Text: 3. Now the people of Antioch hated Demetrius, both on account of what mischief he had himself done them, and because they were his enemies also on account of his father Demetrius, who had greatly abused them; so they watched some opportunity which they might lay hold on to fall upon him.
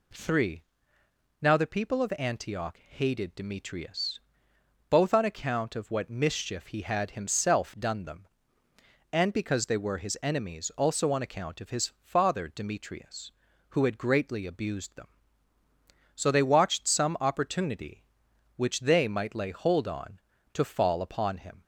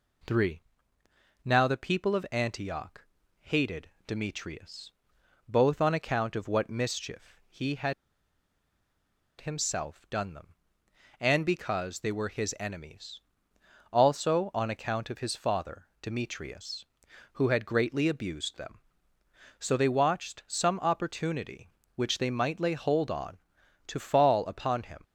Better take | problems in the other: first | pauses between "Antioch" and "hated"; slight; at 3.0 s; 0.36 s long // pauses between "hated" and "Demetrius"; slight; at 3.9 s; 0.16 s long // pauses between "had" and "himself"; strong; at 7.9 s; 1.4 s long // pauses between "enemies" and "also"; noticeable; at 13.2 s; 0.72 s long

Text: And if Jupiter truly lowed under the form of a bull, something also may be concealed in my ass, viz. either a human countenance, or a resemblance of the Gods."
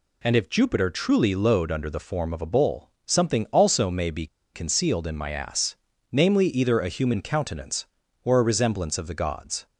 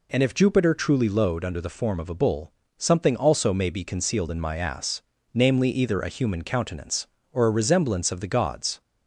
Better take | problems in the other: second | pauses between "be" and "concealed"; slight; at 4.2 s; 0.27 s long

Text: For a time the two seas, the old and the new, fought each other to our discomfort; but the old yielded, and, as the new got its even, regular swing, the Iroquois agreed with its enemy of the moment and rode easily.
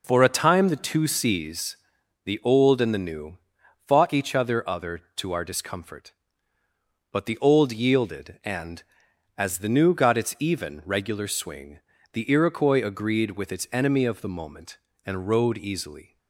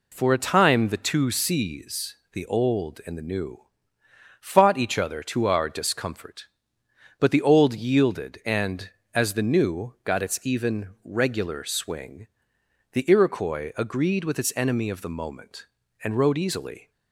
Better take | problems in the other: second | says "other" twice; at 4.6 s

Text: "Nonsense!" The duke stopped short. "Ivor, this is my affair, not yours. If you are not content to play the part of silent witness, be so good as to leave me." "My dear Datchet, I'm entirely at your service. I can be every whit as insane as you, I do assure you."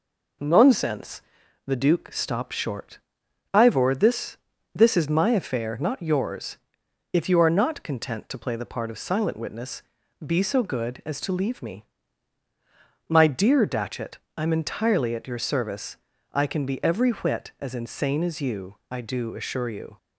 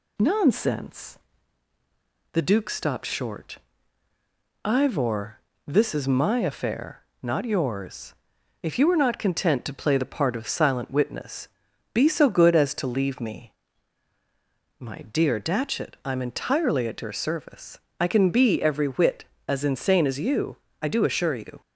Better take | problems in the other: second | says "this" twice; at 4.7 s

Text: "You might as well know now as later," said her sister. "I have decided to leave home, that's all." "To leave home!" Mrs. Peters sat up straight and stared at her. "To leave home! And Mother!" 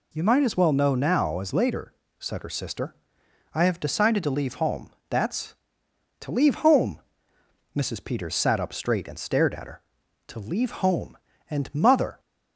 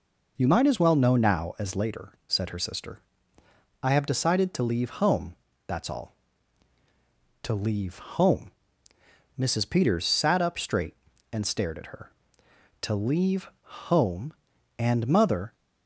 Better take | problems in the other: second | skips "all"; at 5.8 s

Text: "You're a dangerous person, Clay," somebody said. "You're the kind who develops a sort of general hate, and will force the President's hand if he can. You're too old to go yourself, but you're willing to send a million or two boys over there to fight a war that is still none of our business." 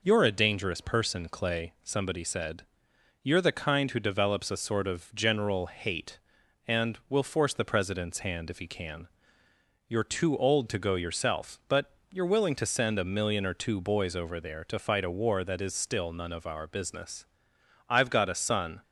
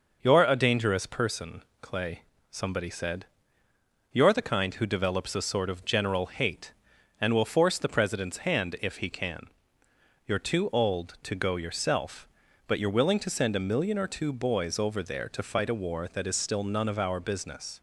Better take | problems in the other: second | pauses between "but" and "you're"; slight; at 11.9 s; 0.18 s long // goes on to say "I've got a son"; noticeable; from 17.8 s on; 0.96 s long

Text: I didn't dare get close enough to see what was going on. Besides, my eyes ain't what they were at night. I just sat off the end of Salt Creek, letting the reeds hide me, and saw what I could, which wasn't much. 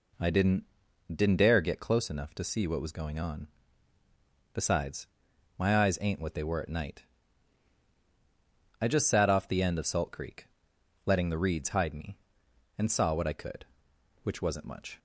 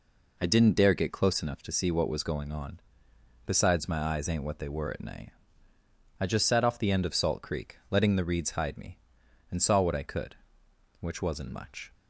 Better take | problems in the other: second | says "didn't" twice; at 1.1 s

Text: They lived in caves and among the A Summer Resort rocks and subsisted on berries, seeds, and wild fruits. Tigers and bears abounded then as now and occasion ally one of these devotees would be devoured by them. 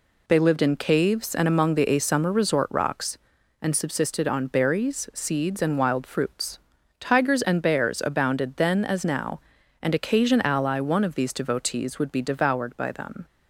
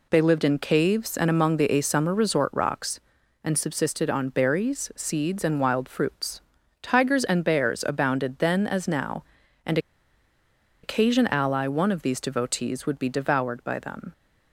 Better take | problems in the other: first | pauses between "and" and "occasion"; at 9.7 s; 1.0 s long

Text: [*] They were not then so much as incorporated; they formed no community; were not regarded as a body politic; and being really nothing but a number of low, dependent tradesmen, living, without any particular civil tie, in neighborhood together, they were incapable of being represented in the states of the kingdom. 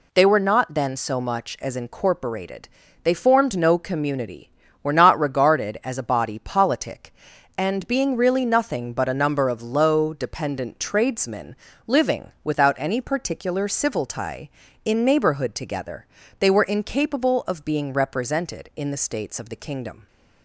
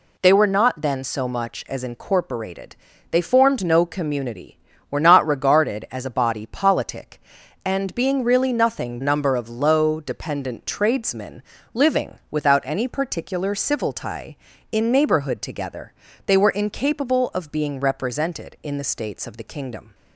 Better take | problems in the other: first | skips "but a"; at 8.9 s

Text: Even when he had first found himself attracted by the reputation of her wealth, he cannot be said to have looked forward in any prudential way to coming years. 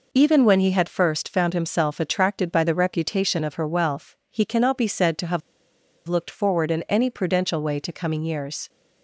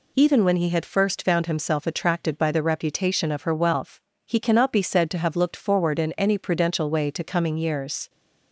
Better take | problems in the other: second | pauses between "have" and "looked"; noticeable; at 5.4 s; 0.68 s long

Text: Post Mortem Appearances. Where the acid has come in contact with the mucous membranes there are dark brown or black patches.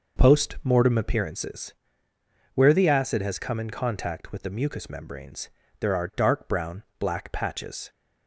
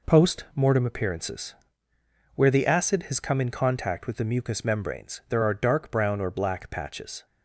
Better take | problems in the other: second | pauses between "membranes" and "there"; slight; at 5.4 s; 0.30 s long // skips "or"; at 6.9 s

